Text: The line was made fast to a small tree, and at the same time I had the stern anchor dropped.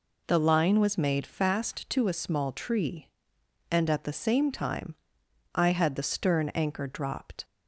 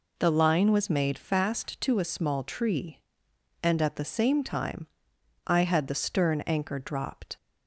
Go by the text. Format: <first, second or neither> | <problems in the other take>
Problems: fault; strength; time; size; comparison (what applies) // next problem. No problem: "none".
neither | pauses between "time" and "I"; noticeable; the same in both